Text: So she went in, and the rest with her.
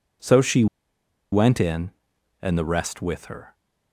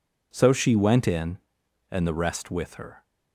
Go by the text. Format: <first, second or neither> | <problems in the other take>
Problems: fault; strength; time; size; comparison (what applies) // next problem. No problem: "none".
second | pauses between "she" and "went"; noticeable; at 0.6 s; 0.66 s long